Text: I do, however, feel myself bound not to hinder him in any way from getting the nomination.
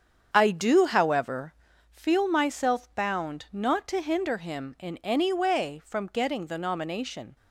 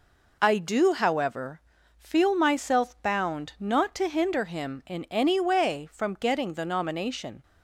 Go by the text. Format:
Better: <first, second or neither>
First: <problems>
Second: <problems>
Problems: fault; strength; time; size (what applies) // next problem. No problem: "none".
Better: second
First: starts louder than the rest; strong; until 2.0 s; 7.5 dB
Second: none